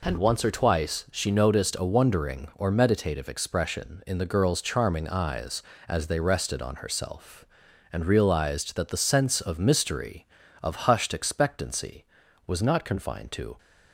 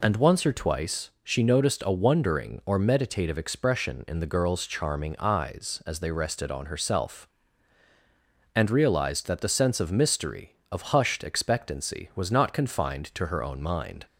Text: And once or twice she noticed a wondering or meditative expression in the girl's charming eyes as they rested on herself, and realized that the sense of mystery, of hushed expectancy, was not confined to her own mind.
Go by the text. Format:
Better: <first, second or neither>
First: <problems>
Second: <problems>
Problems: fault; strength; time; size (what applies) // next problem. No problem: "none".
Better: second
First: stops before "her own mind"; at 13.5 s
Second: none